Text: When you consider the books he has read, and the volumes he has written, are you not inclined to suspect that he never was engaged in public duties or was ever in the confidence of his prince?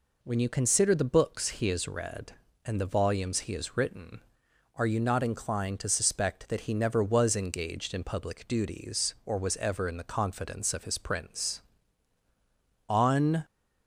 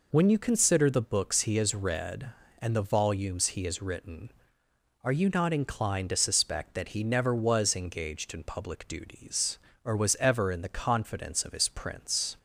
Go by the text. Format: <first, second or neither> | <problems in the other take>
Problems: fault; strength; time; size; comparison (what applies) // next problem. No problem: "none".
second | goes on to say "On"; from 12.8 s on; 0.58 s long